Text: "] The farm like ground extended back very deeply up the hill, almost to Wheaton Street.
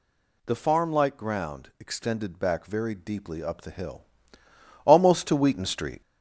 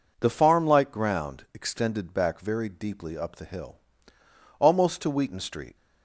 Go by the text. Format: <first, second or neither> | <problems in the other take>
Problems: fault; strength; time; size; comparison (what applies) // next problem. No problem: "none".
second | gets louder; noticeable; throughout; 4 dB